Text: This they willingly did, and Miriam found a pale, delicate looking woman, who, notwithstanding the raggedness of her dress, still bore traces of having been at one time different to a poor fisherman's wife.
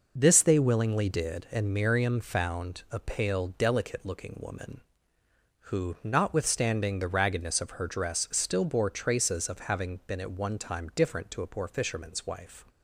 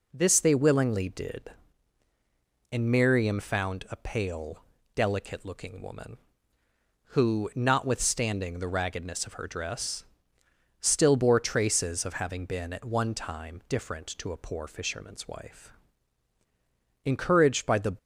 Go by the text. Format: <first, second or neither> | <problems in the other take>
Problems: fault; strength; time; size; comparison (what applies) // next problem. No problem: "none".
first | goes on to say "Encouraged by the"; noticeable; from 17.0 s on; 0.92 s long